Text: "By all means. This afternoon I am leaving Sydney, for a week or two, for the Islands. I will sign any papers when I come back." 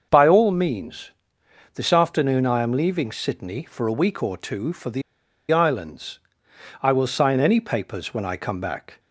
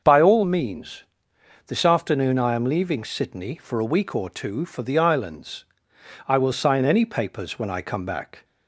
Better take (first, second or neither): second